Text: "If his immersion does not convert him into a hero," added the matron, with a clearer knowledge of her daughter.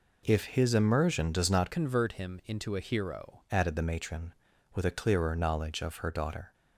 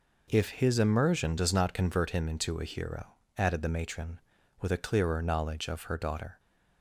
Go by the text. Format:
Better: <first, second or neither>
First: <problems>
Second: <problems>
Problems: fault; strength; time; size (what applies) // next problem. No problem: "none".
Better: second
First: changes voice from "convert" to "hero"; from 1.7 to 3.4 s; 1.7 s long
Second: none